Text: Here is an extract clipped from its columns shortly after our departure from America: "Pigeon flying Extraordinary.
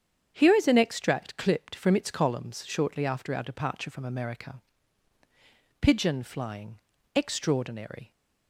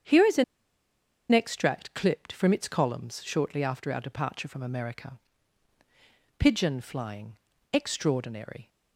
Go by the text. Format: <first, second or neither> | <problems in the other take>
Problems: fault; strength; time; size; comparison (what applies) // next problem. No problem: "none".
first | starts louder than the rest; strong; until 1.9 s; 7.5 dB; strong in the first // pauses between "an" and "extract"; noticeable; at 0.4 s; 0.88 s long // pauses between "flying" and "Extraordinary"; slight; at 7.3 s; 0.36 s long; slight in the first